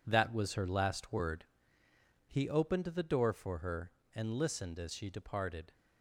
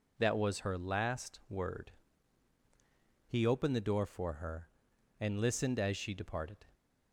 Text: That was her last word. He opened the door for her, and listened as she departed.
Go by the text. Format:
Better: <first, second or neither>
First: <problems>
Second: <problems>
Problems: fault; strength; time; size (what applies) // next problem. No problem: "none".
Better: second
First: gets quieter; strong; throughout; 9 dB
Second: none